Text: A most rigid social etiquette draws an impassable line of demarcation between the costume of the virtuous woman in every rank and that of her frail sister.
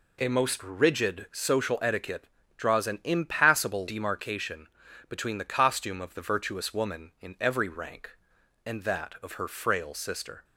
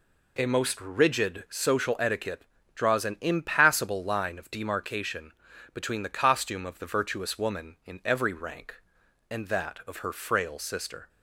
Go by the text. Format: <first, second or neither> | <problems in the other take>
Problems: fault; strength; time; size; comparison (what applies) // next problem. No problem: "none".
second | pauses between "etiquette" and "draws"; slight; at 2.2 s; 0.32 s long; slight in the second // skips "line of"; at 3.8 s // pauses between "demarcation" and "between"; at 4.6 s; 0.42 s long; also in the second